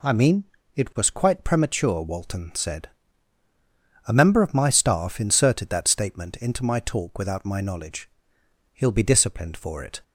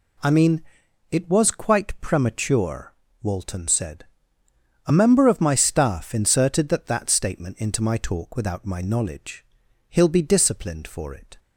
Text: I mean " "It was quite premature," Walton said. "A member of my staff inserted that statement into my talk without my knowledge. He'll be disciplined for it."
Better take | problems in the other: first | says "that" twice; at 6.8 s

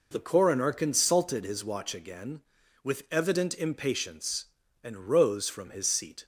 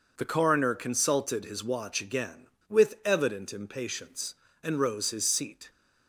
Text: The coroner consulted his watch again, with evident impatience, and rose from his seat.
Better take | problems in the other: first | skips "from"; at 5.1 s

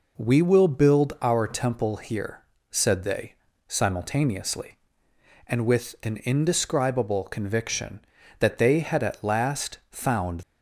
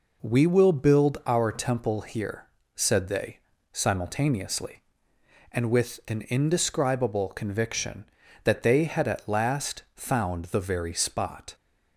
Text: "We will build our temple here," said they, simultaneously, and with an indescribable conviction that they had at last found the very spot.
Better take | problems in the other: second | stops before "the very spot"; at 10.4 s

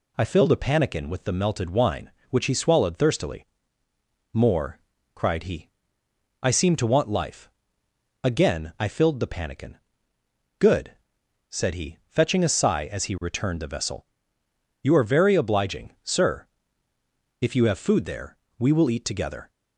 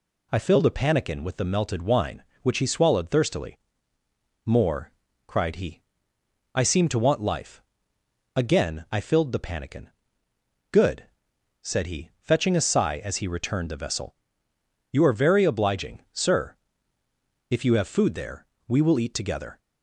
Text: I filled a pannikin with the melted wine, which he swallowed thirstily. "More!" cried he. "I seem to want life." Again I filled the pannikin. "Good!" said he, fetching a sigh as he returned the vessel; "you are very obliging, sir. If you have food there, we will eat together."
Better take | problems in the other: neither | none

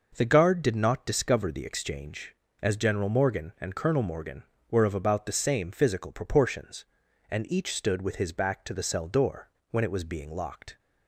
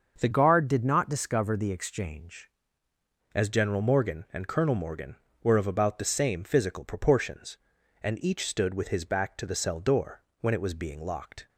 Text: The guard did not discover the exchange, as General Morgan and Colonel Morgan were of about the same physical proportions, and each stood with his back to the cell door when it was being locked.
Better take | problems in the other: first | starts louder than the rest; until 1.2 s; 6.5 dB // changes voice from "guard" to "exchange"; from 0.3 to 2.4 s; 2.1 s long // pauses between "door" and "when"; slight; at 10.2 s; 0.20 s long; slight in the first

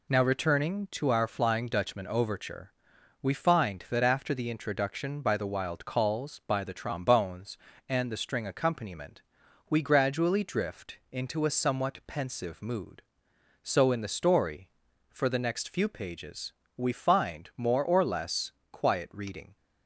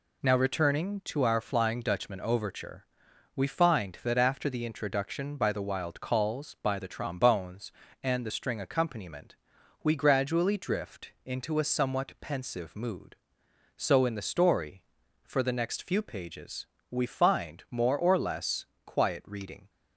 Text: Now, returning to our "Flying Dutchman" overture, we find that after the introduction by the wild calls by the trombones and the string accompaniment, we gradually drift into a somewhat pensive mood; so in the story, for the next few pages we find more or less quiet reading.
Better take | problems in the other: neither | pauses between "pages" and "we"; slight; the same in both // pauses between "less" and "quiet"; slight; the same in both

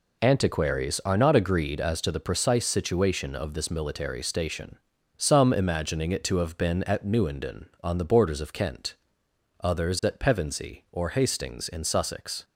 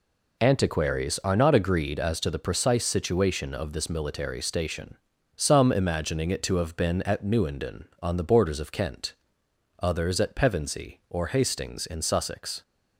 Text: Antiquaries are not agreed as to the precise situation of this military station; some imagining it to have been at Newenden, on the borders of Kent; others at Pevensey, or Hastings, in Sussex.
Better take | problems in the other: neither | none

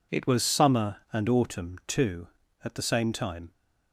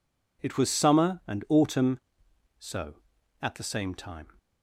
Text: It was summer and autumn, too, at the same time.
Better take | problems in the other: first | says "so" for "too"; at 2.5 s

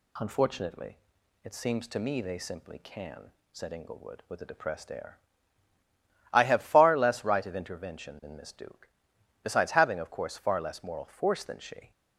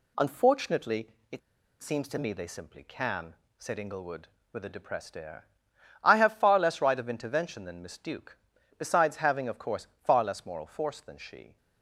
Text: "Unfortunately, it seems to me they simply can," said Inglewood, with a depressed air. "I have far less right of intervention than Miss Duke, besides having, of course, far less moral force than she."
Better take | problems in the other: first | pauses between "it" and "seems"; at 1.4 s; 0.42 s long

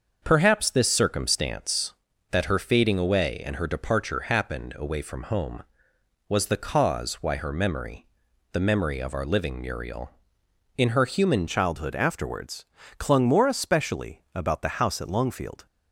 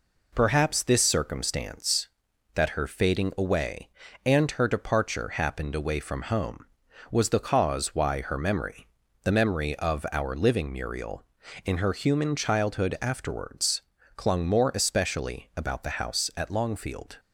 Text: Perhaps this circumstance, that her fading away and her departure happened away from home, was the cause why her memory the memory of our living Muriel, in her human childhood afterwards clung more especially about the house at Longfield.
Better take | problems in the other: second | starts louder than the rest; until 1.2 s; 6.5 dB // pauses between "memory" and "the"; noticeable; at 8.0 s; 0.46 s long; slight in the second // changes voice at "childhood"; from 11.4 s on; 4.2 s long // pauses between "afterwards" and "clung"; slight; at 12.6 s; 0.32 s long; slight in the second

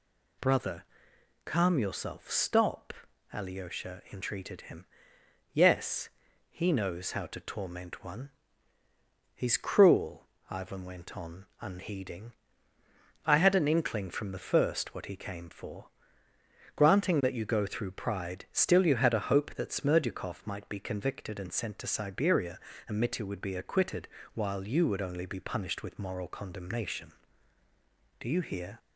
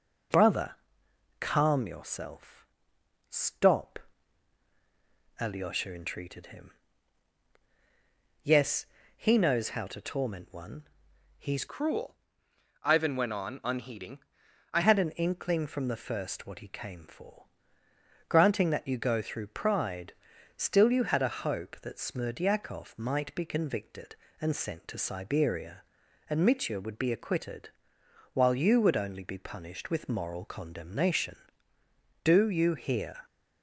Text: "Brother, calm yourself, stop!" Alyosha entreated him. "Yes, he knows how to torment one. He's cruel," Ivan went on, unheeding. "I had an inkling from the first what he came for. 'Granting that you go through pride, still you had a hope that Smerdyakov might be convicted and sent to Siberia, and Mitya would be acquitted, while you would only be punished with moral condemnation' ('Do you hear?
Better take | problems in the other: first | changes voice from "cruel" to "I"; from 11.6 to 14.8 s; 3.2 s long

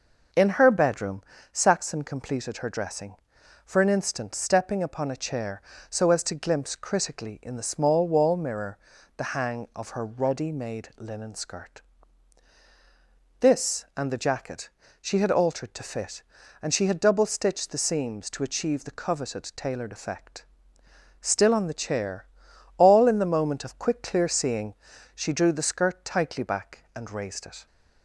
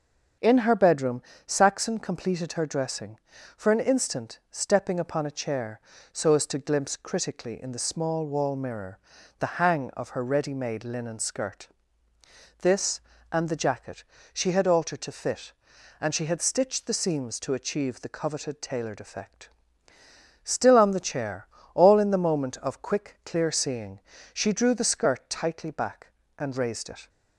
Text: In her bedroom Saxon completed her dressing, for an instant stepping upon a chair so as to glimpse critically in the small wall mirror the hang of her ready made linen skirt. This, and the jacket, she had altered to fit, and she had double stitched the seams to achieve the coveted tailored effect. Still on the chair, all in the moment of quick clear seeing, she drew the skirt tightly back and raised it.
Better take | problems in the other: first | starts louder than the rest; until 1.6 s; 7 dB // pauses between "bedroom" and "Saxon"; slight; at 1.2 s; 0.24 s long; slight in the first // pauses between "mirror" and "the"; at 8.9 s; 0.40 s long; also in the first // skips "double"; at 16.4 s

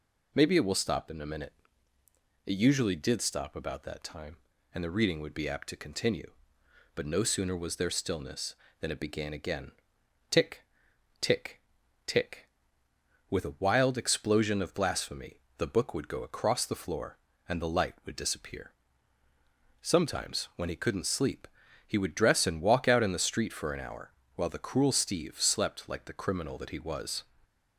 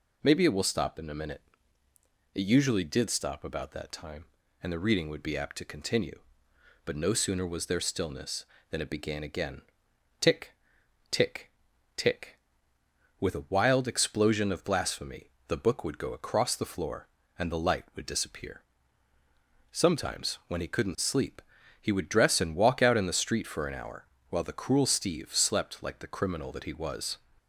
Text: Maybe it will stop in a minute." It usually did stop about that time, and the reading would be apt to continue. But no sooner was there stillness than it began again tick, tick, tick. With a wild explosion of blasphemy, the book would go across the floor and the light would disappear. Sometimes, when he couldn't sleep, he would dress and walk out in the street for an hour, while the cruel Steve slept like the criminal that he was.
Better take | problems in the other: neither | pauses between "again" and "tick"; noticeable; the same in both

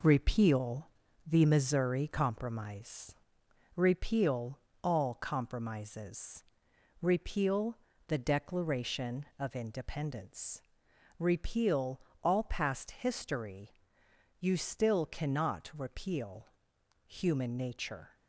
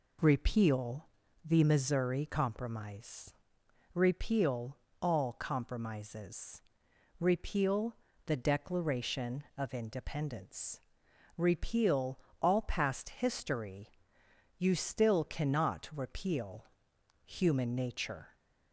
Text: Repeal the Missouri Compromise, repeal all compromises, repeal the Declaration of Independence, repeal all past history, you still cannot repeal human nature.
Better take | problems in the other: second | gets quieter; noticeable; throughout; 5.5 dB // pauses between "Repeal" and "the"; at 0.8 s; 0.42 s long; also in the second // pauses between "repeal" and "all"; slight; at 4.5 s; 0.26 s long; slight in the second // pauses between "repeal" and "the"; slight; at 7.7 s; 0.30 s long; slight in the second // pauses between "repeal" and "all"; slight; at 12.0 s; 0.22 s long; slight in the second // pauses between "repeal" and "human"; noticeable; at 16.4 s; 0.58 s long; noticeable in the second

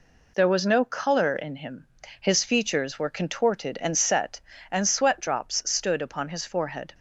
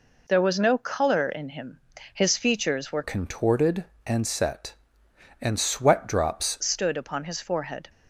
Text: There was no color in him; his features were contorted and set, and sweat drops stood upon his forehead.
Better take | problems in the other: first | changes voice from "contorted" to "drops"; from 3.0 to 6.5 s; 3.5 s long

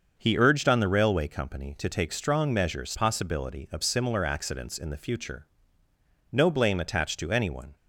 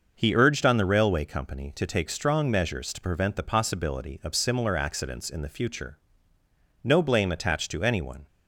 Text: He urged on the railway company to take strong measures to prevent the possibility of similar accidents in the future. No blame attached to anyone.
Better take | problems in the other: second | starts louder than the rest; until 1.1 s; 6.5 dB // skips "to prevent the"; at 2.9 s

